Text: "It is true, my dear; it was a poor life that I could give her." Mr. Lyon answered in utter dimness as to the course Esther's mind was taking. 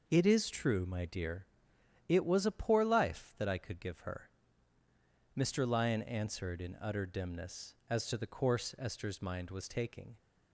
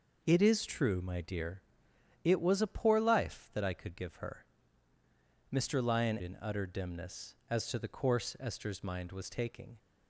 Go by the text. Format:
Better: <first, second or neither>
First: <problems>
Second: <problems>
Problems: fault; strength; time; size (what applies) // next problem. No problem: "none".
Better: first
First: none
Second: skips "answered"; at 6.2 s